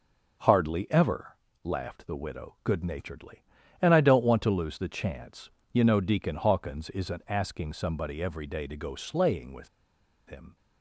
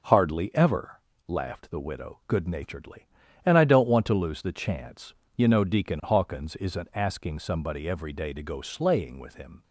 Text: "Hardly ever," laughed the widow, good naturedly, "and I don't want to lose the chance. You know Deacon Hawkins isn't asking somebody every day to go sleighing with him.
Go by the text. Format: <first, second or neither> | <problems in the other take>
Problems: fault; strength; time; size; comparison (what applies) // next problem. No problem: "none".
second | pauses between "with" and "him"; noticeable; at 9.6 s; 0.58 s long